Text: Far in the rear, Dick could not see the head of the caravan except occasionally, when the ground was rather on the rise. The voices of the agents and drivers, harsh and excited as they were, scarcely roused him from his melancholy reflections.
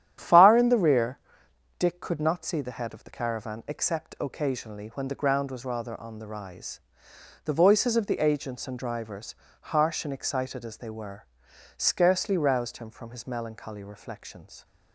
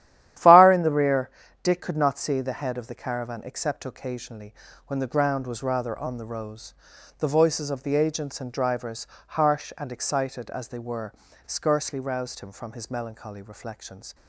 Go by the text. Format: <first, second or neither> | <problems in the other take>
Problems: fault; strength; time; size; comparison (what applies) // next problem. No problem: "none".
first | starts louder than the rest; strong; until 1.7 s; 12 dB; strong in the first // says "rose" for "rise"; at 6.2 s